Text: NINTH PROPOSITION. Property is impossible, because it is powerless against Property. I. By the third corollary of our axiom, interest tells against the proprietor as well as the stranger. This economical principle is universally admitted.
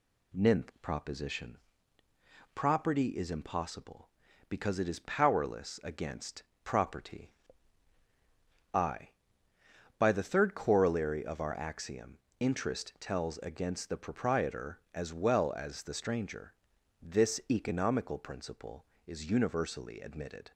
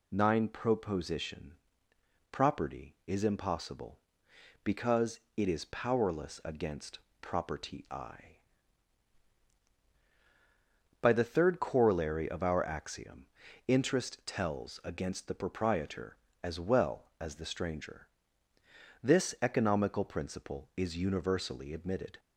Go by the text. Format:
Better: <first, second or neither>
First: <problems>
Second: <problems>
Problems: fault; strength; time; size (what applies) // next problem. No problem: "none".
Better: first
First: pauses between "against" and "Property"; slight; at 6.4 s; 0.22 s long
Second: says "Nine" for "NINTH"; at 0.1 s // pauses between "because" and "it"; slight; at 5.1 s; 0.16 s long // pauses between "against" and "Property"; slight; at 6.9 s; 0.20 s long